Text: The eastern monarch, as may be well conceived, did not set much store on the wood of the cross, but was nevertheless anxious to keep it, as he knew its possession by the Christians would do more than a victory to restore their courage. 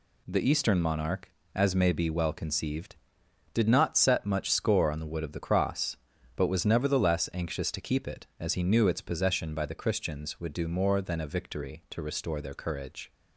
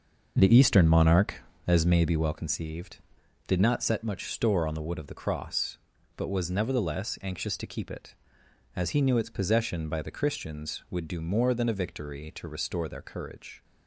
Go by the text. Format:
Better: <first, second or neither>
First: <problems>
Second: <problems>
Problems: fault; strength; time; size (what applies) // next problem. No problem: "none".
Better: second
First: says "score" for "store"; at 4.4 s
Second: none